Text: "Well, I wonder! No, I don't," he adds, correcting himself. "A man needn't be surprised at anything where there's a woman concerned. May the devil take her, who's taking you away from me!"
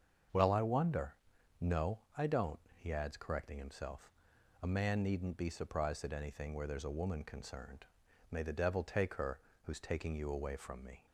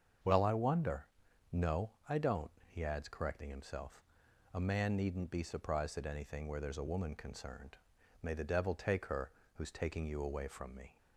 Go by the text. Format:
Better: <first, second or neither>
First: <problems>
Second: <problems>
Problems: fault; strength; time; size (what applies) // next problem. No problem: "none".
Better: neither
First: starts louder than the rest; until 1.7 s; 7 dB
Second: starts louder than the rest; until 1.6 s; 7 dB